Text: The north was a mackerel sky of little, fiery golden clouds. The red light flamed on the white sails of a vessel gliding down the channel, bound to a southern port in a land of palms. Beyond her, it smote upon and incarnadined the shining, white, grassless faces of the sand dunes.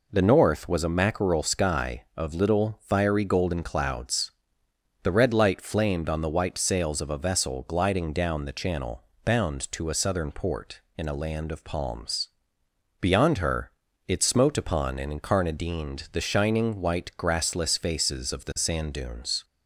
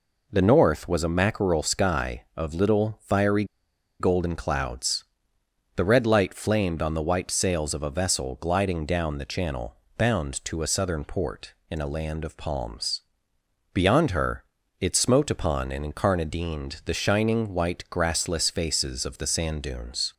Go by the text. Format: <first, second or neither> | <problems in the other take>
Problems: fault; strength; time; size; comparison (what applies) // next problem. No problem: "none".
first | pauses between "fiery" and "golden"; noticeable; at 3.4 s; 0.55 s long